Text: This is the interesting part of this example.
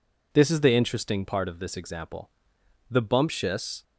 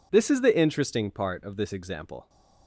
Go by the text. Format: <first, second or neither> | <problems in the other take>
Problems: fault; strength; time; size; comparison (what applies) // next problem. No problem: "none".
second | goes on to say "The bumptious"; noticeable; from 2.8 s on; 0.94 s long